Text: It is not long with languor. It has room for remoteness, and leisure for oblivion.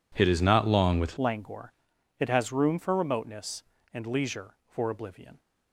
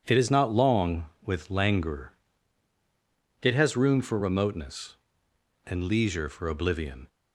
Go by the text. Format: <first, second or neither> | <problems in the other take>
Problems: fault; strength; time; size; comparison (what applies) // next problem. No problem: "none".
second | changes voice at "languor"; from 1.1 s on; 4.2 s long